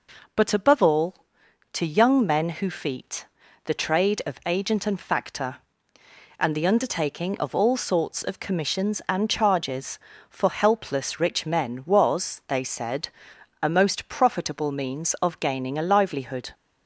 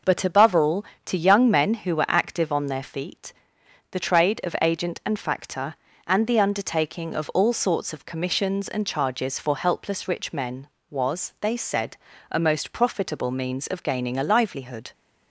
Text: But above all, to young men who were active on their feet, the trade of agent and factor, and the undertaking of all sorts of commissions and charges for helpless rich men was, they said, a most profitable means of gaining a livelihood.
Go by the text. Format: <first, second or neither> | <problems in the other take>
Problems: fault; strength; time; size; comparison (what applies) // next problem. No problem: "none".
second | skips "were active on their"; at 2.6 s